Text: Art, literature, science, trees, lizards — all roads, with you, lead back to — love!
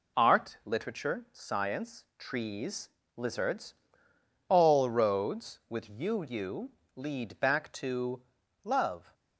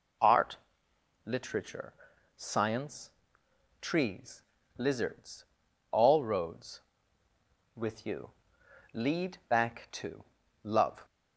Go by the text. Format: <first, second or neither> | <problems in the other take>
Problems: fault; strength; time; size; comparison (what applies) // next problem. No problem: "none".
second | says "you" twice; at 6.2 s